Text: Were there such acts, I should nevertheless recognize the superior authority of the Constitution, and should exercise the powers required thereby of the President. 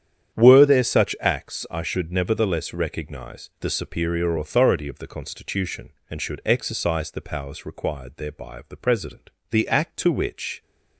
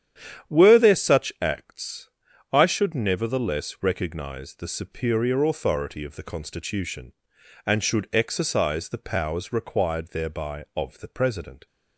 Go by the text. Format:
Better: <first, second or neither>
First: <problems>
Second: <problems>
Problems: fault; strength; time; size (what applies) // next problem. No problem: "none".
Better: second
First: starts louder than the rest; strong; until 1.4 s; 9 dB // goes on to say "The act to which"; noticeable; from 9.4 s on; 1.1 s long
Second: starts louder than the rest; strong; until 1.5 s; 9.5 dB